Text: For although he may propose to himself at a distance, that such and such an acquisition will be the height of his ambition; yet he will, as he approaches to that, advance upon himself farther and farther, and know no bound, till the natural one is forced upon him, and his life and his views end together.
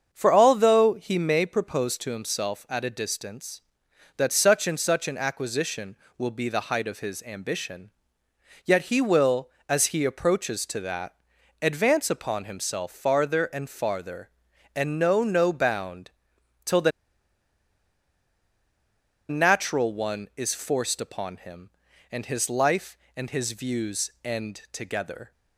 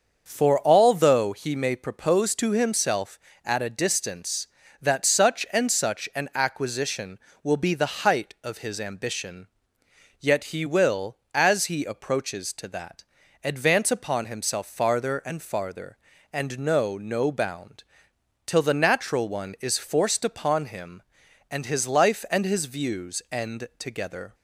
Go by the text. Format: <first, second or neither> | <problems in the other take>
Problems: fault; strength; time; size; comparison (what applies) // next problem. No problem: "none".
second | starts louder than the rest; until 1.1 s; 7 dB; also in the second // pauses between "the" and "natural"; strong; at 16.9 s; 2.3 s long